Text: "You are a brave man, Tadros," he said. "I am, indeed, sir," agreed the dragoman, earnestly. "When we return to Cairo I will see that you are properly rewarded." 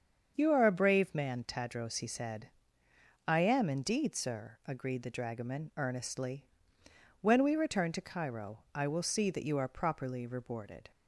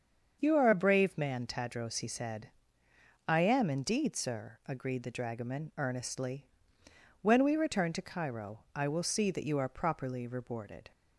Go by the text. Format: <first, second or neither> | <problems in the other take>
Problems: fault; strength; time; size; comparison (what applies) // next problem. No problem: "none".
neither | starts louder than the rest; the same in both // pauses between "Cairo" and "I"; slight; the same in both